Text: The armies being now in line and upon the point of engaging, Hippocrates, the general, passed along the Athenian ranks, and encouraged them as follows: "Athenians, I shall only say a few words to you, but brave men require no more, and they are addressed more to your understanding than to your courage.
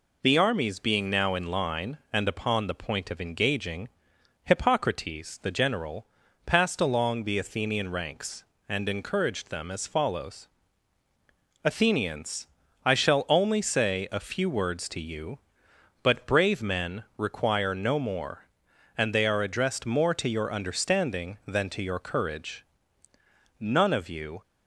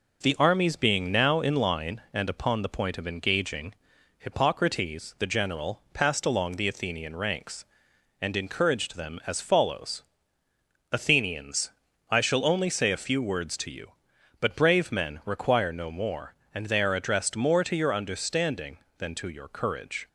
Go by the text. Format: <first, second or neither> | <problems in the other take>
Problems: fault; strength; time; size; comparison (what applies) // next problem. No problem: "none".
second | pauses between "men" and "require"; slight; at 17.0 s; 0.16 s long // goes on to say "None of you"; noticeable; from 23.5 s on; 0.82 s long